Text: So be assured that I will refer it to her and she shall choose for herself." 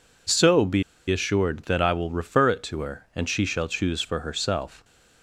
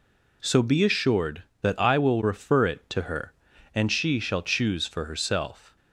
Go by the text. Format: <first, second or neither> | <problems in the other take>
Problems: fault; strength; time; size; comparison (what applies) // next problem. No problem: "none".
second | pauses between "be" and "assured"; slight; at 0.8 s; 0.27 s long